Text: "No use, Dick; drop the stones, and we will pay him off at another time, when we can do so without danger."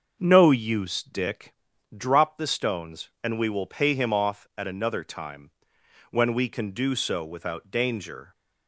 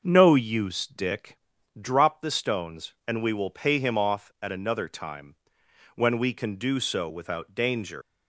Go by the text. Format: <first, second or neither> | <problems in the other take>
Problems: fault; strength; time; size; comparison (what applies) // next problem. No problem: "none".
first | starts louder than the rest; noticeable; until 1.0 s; 6 dB; also in the first // leaves "danger" unfinished; at 8.0 s; 165 ms